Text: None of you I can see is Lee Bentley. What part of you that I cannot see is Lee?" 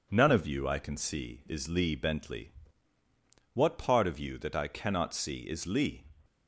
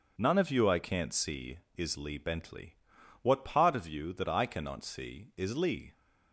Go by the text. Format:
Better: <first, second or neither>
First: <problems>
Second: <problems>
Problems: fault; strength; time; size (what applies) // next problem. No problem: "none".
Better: first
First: none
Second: says "can't" for "can"; at 0.8 s